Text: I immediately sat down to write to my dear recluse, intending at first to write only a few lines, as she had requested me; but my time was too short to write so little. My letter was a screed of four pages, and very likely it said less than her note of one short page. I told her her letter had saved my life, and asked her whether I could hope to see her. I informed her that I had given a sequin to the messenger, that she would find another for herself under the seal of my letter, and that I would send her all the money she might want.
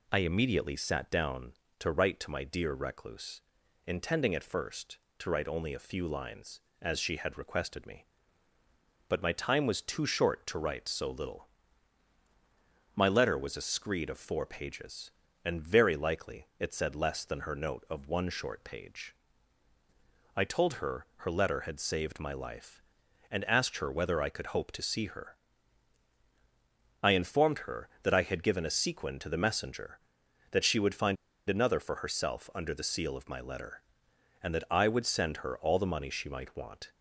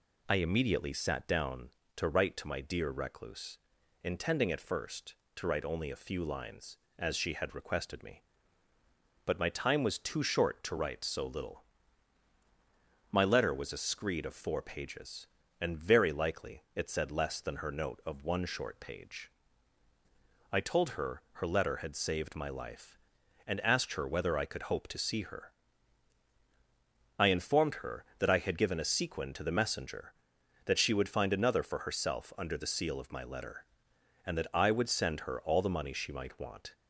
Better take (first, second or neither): second